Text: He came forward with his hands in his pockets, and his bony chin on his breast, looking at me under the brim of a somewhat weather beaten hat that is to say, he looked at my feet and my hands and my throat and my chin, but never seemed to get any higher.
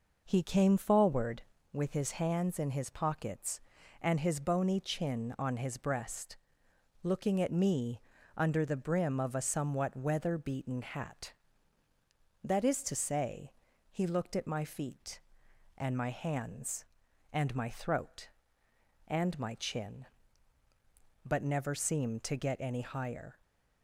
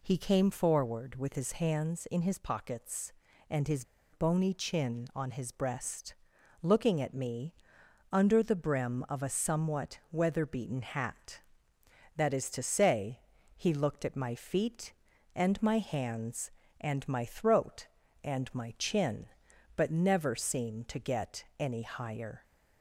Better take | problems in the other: first | pauses between "his" and "bony"; slight; at 3.8 s; 0.29 s long // pauses between "me" and "under"; noticeable; at 7.5 s; 0.58 s long; slight in the first

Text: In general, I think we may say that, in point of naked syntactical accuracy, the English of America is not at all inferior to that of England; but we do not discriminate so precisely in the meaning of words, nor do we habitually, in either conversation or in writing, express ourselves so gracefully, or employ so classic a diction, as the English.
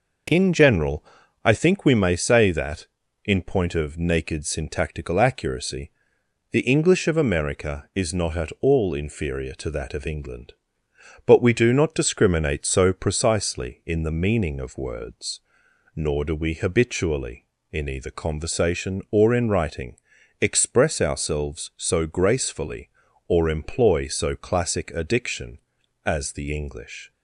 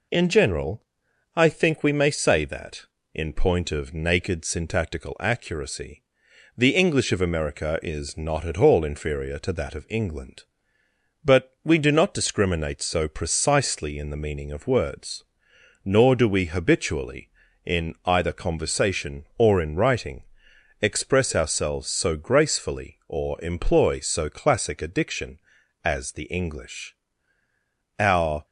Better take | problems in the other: first | goes on to say "Our"; slight; from 27.9 s on; 0.46 s long

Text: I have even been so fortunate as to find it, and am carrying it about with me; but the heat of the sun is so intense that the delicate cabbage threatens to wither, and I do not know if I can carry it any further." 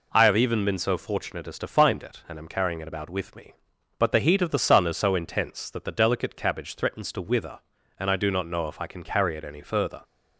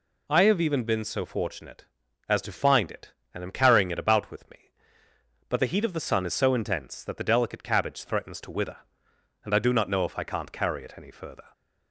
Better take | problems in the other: first | says "can't" for "can"; at 10.2 s

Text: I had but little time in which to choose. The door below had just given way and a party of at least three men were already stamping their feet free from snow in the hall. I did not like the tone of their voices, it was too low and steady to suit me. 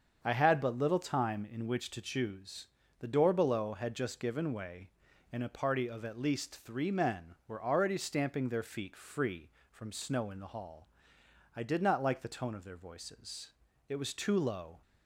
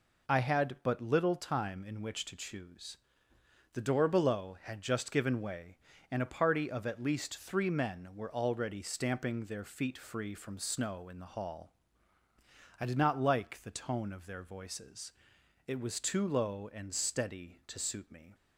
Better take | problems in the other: second | starts louder than the rest; strong; until 1.2 s; 7 dB // stops before "and steady to suit me"; at 14.8 s

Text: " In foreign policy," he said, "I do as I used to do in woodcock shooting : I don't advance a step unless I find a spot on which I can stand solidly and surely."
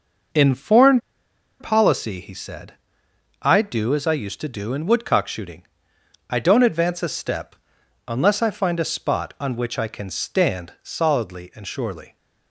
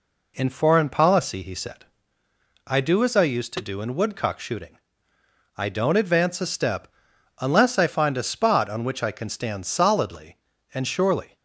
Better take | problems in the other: second | starts louder than the rest; noticeable; until 1.9 s; 6 dB // pauses between "foreign" and "policy"; noticeable; at 0.9 s; 0.61 s long // pauses between "step" and "unless"; noticeable; at 7.5 s; 0.50 s long; noticeable in the second

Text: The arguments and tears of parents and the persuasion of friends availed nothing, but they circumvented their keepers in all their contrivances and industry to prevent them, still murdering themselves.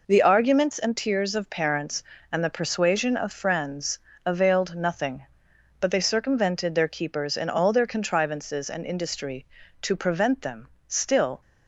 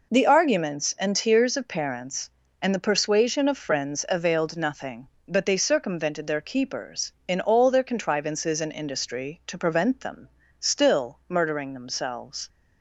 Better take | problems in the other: second | pauses between "friends" and "availed"; slight; at 3.9 s; 0.26 s long // stops before "murdering themselves"; at 11.4 s

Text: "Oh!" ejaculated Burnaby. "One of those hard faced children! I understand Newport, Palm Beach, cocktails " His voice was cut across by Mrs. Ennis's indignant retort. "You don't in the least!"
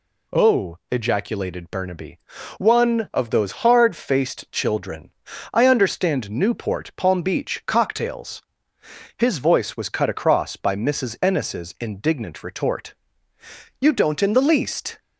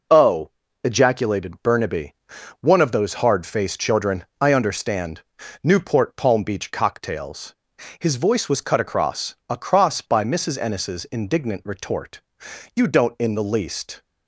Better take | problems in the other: first | pauses between "understand" and "Newport"; at 5.2 s; 0.42 s long // says "across" twice; at 9.4 s

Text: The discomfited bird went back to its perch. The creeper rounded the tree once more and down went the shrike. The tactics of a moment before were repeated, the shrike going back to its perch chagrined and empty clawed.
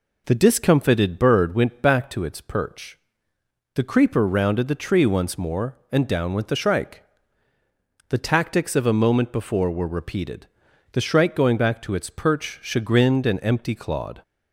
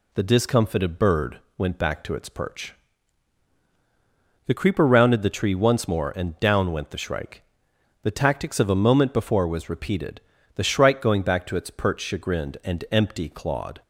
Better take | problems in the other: first | pauses between "bird" and "went"; slight; at 1.3 s; 0.18 s long // says "was" for "were"; at 9.4 s

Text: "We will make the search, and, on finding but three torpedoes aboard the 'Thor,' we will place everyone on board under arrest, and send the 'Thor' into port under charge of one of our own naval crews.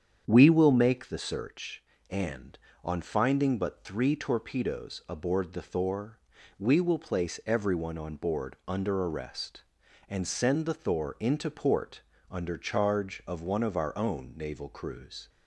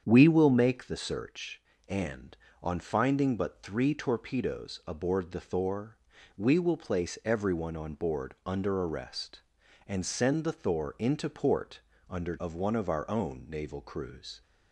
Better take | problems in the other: first | starts louder than the rest; strong; until 1.0 s; 8 dB; strong in the first // pauses between "port" and "under"; slight; at 11.7 s; 0.30 s long; slight in the first // skips "charge"; at 12.3 s

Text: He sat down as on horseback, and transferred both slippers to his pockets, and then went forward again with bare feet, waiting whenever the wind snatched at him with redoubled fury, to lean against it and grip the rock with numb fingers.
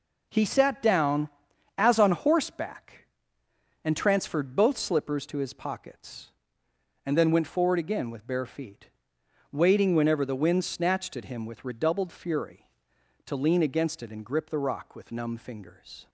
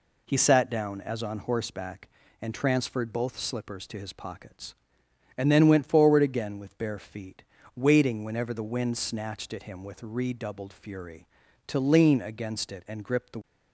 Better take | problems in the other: first | stops before "rock with numb fingers"; at 13.4 s

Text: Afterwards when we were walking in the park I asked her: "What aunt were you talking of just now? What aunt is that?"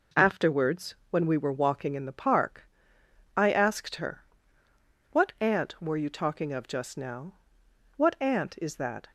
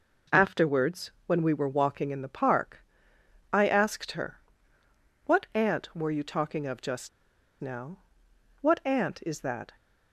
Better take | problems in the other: first | pauses between "park" and "I"; noticeable; at 2.8 s; 0.66 s long; noticeable in the first // pauses between "just" and "now"; noticeable; at 7.0 s; 0.51 s long

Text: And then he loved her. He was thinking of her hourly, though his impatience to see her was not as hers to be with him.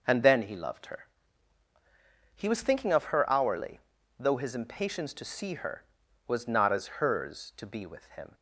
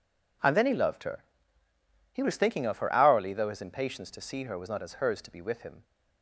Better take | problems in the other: neither | none

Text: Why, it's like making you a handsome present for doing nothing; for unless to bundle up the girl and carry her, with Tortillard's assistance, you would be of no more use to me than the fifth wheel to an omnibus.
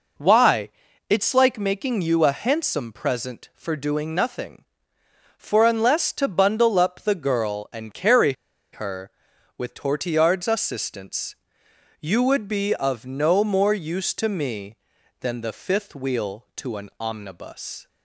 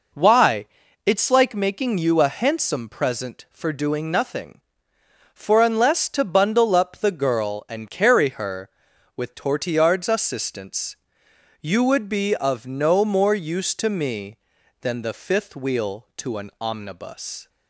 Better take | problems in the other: second | pauses between "carry" and "her"; at 8.3 s; 0.40 s long

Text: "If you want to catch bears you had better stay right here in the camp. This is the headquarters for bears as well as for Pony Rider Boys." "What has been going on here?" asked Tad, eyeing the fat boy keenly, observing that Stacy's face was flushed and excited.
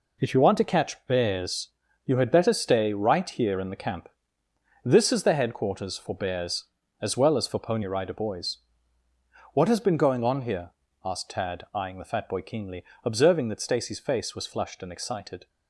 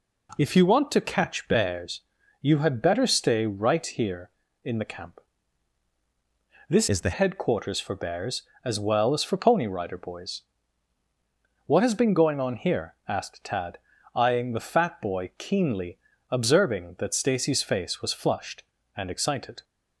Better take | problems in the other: first | pauses between "bears" and "you"; at 2.0 s; 0.38 s long; slight in the first // changes voice from "is" to "the"; from 6.8 to 7.1 s; 0.3 s long

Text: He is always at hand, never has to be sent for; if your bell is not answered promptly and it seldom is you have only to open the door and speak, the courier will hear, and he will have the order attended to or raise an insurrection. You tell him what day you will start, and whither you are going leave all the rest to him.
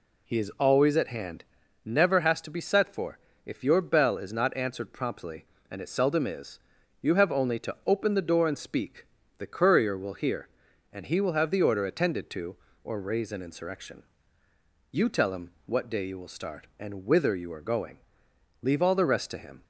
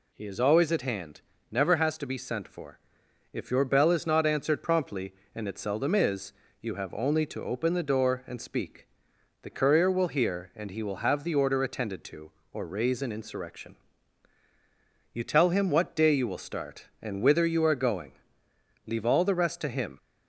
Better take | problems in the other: second | says "set" for "sent"; at 2.6 s // pauses between "is" and "you"; at 6.5 s; 0.42 s long; slight in the second // pauses between "him" and "what"; slight; at 15.5 s; 0.16 s long // pauses between "going" and "leave"; noticeable; at 17.9 s; 0.64 s long; noticeable in the second

